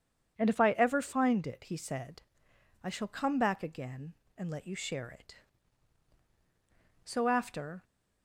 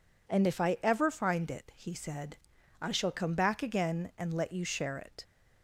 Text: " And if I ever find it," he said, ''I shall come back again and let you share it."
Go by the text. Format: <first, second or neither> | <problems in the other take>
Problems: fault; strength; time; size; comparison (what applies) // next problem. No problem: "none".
second | goes on to say "So after"; noticeable; from 7.0 s on; 0.78 s long